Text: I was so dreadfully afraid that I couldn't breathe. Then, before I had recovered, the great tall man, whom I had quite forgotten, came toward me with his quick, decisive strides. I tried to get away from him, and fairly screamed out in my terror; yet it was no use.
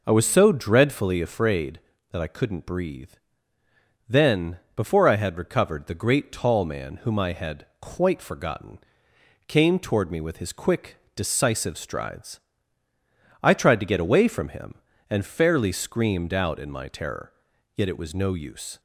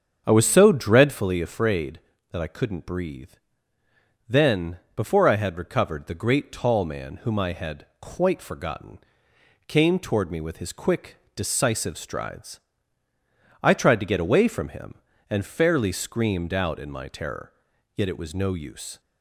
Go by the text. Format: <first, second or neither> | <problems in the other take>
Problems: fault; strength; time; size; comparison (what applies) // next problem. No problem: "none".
first | starts louder than the rest; strong; until 1.2 s; 7.5 dB // pauses between "had" and "quite"; slight; at 7.8 s; 0.16 s long; slight in the first